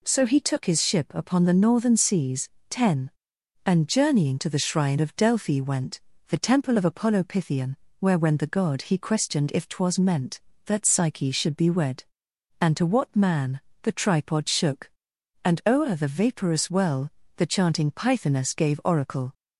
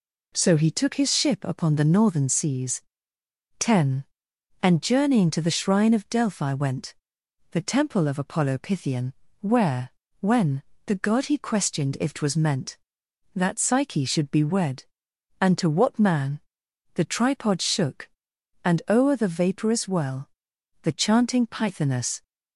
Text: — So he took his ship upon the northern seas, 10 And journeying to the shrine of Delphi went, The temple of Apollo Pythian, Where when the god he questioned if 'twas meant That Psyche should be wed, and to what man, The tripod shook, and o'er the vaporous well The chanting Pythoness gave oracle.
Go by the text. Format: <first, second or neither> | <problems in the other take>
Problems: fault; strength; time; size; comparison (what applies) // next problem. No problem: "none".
first | pauses between "Where" and "when"; slight; at 9.9 s; 0.30 s long // pauses between "when" and "the"; slight; at 10.6 s; 0.24 s long // pauses between "well" and "The"; noticeable; at 20.3 s; 0.50 s long; slight in the first // stops before "gave oracle"; at 22.2 s